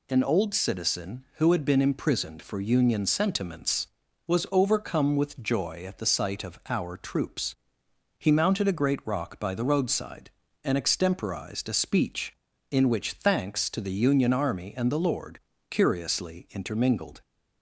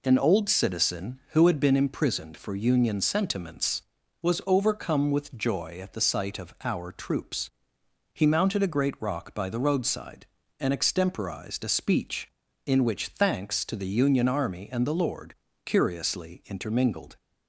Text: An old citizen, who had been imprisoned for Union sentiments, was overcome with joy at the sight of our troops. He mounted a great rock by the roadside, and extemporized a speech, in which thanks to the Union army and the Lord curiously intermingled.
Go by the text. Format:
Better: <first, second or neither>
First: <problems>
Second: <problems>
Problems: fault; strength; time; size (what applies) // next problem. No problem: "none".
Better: first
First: pauses between "Lord" and "curiously"; slight; at 15.3 s; 0.30 s long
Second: starts louder than the rest; slight; until 1.9 s; 3.5 dB // pauses between "Lord" and "curiously"; slight; at 15.3 s; 0.30 s long